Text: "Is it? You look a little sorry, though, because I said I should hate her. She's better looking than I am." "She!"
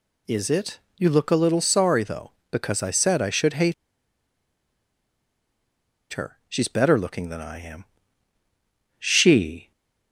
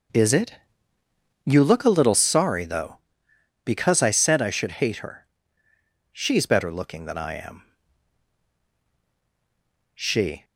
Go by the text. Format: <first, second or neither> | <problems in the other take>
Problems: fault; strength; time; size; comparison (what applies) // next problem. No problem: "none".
second | pauses between "hate" and "her"; strong; at 3.7 s; 2.3 s long